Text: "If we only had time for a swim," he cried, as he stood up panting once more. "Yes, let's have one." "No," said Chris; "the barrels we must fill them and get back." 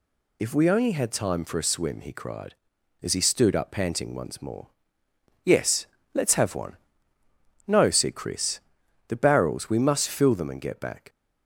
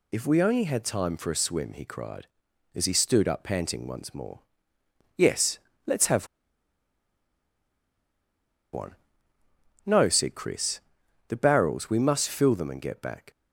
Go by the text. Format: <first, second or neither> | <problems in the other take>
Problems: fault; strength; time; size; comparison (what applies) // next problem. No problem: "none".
first | pauses between "have" and "one"; strong; at 6.2 s; 2.4 s long